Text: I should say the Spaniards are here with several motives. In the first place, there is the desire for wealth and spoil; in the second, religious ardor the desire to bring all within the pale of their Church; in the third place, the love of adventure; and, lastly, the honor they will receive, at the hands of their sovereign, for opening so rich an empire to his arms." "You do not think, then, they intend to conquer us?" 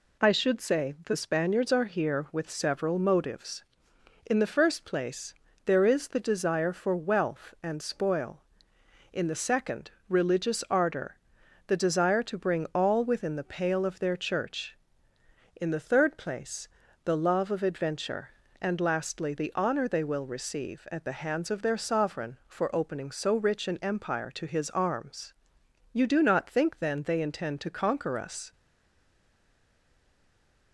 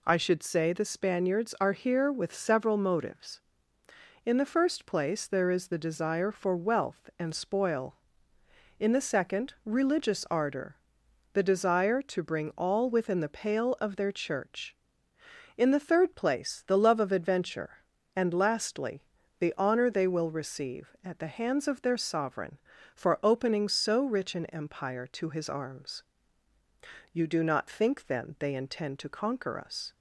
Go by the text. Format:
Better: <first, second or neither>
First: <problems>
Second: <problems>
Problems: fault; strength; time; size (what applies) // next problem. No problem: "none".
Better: second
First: pauses between "ardor" and "the"; noticeable; at 11.1 s; 0.50 s long // stays silent after the last word; from 28.5 s on; 2.2 s long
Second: pauses between "ardor" and "the"; noticeable; at 10.7 s; 0.56 s long